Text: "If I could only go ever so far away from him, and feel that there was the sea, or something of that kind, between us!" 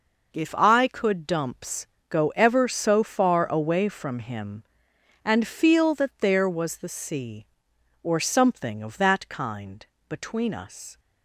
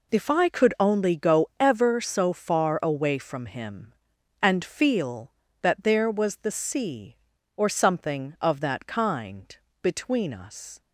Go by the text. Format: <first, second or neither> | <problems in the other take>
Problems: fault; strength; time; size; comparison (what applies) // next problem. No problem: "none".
second | says "dumps" for "only"; at 1.2 s